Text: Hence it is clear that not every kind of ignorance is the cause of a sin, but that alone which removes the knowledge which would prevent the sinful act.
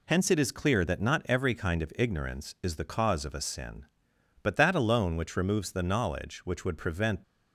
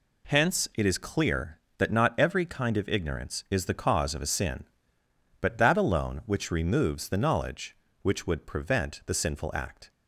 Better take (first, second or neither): second